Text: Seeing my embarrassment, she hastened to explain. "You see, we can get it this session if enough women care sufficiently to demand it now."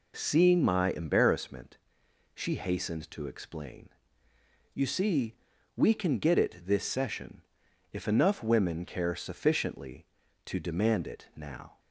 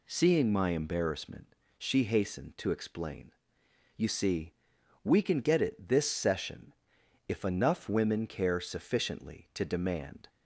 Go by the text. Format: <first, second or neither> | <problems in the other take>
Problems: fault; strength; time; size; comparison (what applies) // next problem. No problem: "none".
first | pauses between "session" and "if"; noticeable; at 6.7 s; 0.52 s long; noticeable in the first // stops before "it now"; at 10.2 s